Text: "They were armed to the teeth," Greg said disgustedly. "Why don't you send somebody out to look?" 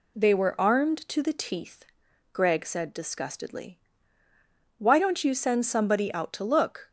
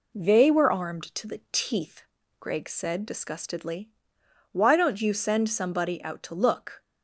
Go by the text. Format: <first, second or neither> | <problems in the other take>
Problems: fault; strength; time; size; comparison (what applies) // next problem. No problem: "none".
first | starts louder than the rest; slight; until 1.9 s; 3 dB